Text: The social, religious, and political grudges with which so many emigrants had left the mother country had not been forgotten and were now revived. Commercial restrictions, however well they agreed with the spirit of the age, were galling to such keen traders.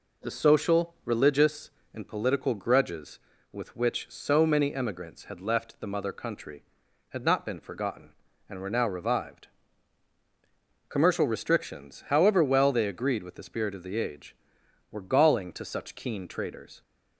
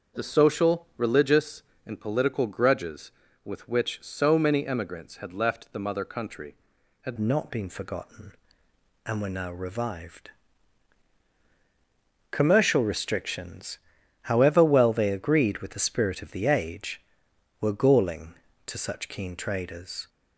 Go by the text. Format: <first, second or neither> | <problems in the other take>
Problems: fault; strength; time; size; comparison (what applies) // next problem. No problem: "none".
first | starts louder than the rest; until 1.2 s; 6.5 dB // changes voice at "not"; from 7.1 s on; 12.9 s long